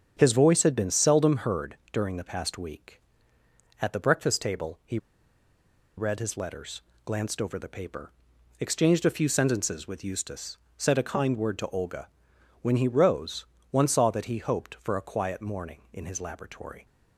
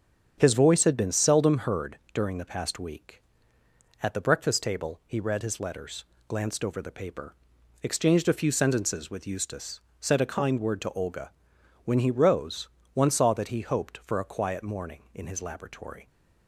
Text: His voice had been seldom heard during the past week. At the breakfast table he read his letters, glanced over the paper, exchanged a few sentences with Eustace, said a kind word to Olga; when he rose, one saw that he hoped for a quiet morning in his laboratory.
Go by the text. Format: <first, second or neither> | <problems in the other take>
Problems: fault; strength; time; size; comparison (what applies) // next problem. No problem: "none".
second | starts louder than the rest; strong; until 1.1 s; 8 dB; strong in the second // pauses between "he" and "read"; at 4.9 s; 0.99 s long